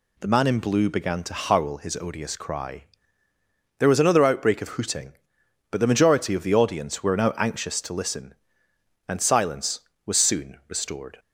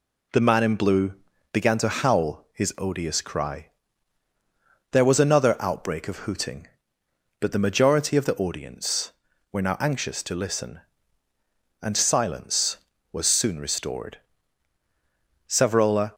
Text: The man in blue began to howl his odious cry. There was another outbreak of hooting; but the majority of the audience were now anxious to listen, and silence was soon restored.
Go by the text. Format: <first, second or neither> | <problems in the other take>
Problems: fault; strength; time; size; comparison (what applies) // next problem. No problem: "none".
first | pauses between "blue" and "began"; at 1.1 s; 0.38 s long // goes on to say "Savrola"; noticeable; from 15.4 s on; 0.66 s long